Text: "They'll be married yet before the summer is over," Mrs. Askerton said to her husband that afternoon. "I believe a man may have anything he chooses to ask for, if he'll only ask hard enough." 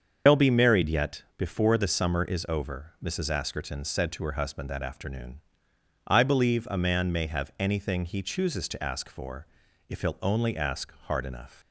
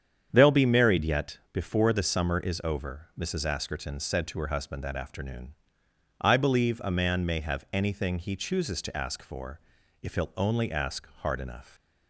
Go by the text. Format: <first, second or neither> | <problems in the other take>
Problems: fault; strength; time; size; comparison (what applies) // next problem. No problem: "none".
second | loses the start of "They'll"; at 0.2 s; 90 ms // starts louder than the rest; until 1.4 s; 7 dB; strong in the second // pauses between "ask" and "hard"; slight; at 10.9 s; 0.16 s long; slight in the second